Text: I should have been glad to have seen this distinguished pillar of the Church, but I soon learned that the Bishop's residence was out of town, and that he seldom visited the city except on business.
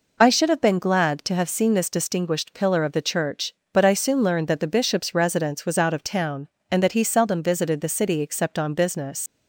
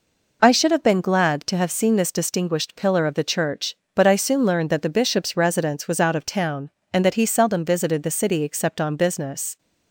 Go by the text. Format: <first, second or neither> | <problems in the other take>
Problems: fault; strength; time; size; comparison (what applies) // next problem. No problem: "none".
second | leaves "business" unfinished; at 9.2 s; 95 ms